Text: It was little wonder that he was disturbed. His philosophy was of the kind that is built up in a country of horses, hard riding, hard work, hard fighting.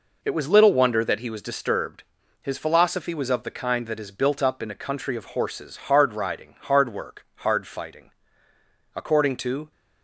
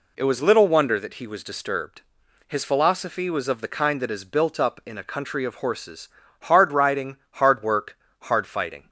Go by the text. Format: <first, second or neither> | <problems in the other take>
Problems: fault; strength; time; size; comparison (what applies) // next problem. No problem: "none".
second | goes on to say "According to"; noticeable; from 8.9 s on; 0.76 s long